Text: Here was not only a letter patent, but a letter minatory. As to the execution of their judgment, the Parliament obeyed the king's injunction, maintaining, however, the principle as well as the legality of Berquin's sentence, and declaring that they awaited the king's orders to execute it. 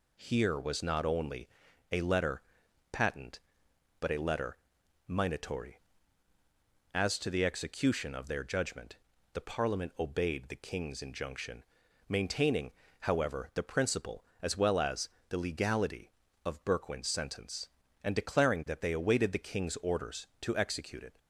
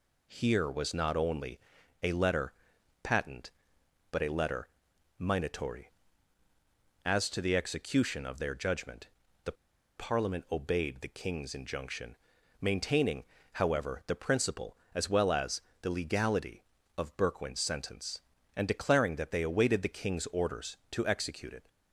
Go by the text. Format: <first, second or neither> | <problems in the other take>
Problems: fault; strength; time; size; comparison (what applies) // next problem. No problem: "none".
first | pauses between "only" and "a"; at 1.5 s; 0.44 s long; also in the first // pauses between "letter" and "patent"; noticeable; at 2.5 s; 0.50 s long; noticeable in the first // pauses between "letter" and "minatory"; noticeable; at 4.6 s; 0.50 s long; noticeable in the first // pauses between "the" and "Parliament"; at 9.5 s; 0.44 s long // pauses between "as" and "the"; slight; at 15.5 s; 0.22 s long; slight in the first